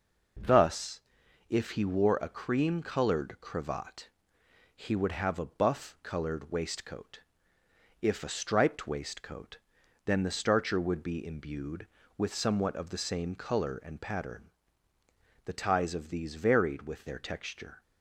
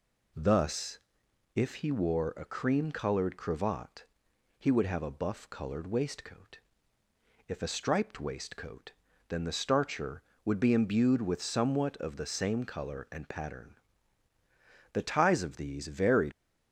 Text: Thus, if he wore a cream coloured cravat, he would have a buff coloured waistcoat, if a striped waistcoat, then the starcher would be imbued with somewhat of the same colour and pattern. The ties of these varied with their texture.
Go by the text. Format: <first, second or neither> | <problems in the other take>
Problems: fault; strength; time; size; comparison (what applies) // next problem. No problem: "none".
first | stops before "with their texture"; at 16.3 s